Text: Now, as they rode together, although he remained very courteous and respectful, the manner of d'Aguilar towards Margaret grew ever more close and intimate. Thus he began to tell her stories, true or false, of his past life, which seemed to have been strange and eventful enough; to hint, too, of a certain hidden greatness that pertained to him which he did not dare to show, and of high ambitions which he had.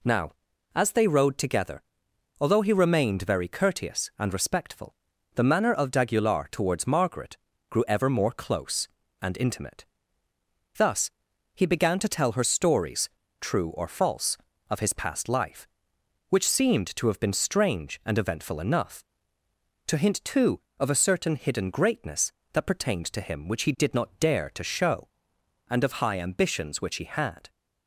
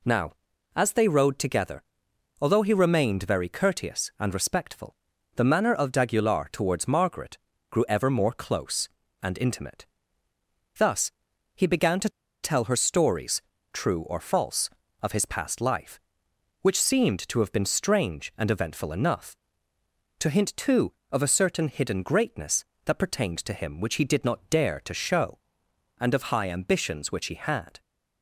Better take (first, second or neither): first